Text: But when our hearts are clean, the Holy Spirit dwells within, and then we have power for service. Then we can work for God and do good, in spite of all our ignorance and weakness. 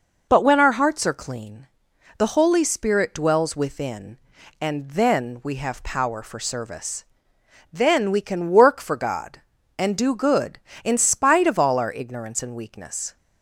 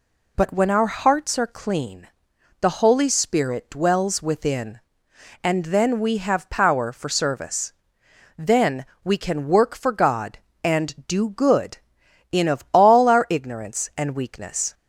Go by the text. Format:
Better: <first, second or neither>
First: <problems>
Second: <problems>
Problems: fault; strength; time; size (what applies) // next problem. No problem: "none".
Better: first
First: none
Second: pauses between "Then" and "we"; slight; at 8.8 s; 0.18 s long // skips "spite"; at 12.4 s